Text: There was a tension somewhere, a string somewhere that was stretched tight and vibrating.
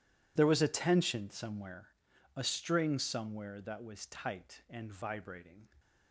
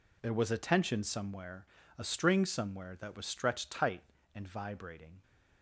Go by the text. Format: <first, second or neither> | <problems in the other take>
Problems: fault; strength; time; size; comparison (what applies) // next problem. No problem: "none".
second | skips "stretched"; at 4.0 s